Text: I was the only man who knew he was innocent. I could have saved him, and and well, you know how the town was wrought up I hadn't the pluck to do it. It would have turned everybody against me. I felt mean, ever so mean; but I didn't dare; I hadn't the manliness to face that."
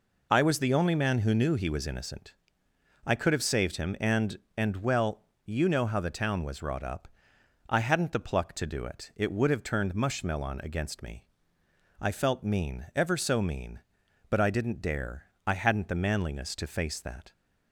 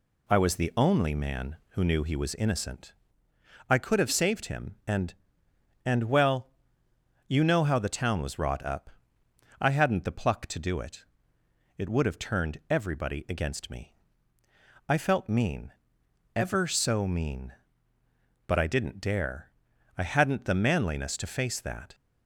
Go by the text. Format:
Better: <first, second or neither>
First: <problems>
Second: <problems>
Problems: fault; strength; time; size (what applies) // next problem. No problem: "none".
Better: second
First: pauses between "up" and "I"; noticeable; at 7.0 s; 0.60 s long // says "mushmelon" for "everybody"; at 9.9 s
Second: pauses between "up" and "I"; noticeable; at 8.9 s; 0.70 s long